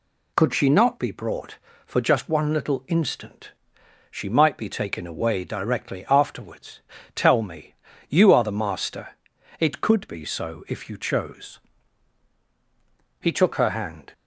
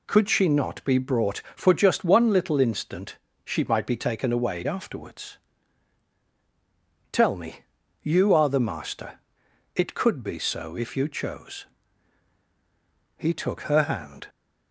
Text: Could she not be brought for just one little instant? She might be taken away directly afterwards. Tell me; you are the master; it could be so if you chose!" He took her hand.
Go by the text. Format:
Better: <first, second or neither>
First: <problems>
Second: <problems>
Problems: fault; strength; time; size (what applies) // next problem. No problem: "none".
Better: first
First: none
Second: skips "directly"; at 4.6 s